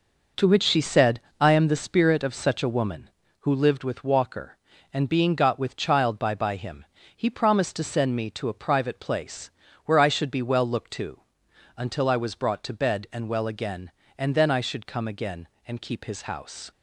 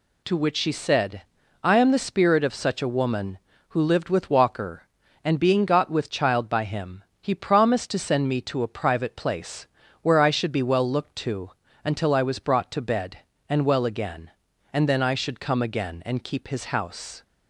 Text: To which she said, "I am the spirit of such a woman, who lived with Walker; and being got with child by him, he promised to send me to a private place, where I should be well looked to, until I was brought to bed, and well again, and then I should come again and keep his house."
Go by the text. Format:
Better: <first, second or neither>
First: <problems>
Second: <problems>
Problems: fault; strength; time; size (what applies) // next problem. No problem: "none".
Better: second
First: says "by" twice; at 6.3 s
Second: none